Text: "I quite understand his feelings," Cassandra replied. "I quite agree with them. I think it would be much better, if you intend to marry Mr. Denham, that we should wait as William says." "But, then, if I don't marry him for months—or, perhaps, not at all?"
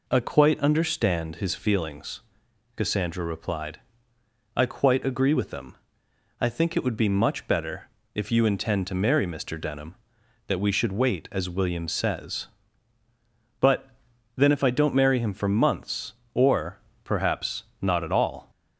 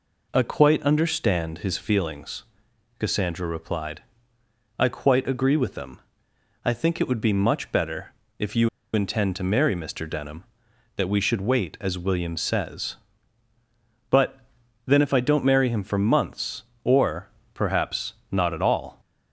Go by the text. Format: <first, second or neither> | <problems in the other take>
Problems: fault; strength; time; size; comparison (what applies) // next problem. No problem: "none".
first | pauses between "you" and "intend"; slight; at 8.6 s; 0.24 s long